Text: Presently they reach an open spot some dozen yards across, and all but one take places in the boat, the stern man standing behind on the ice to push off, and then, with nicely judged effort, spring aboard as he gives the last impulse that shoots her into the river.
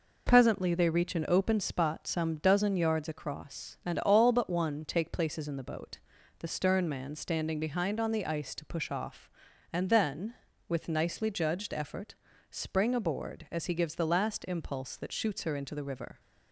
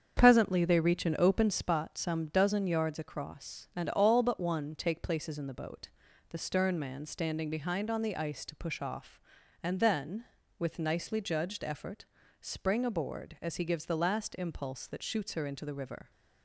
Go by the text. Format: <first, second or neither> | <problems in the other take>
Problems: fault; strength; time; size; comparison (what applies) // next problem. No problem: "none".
first | starts louder than the rest; strong; until 1.7 s; 7.5 dB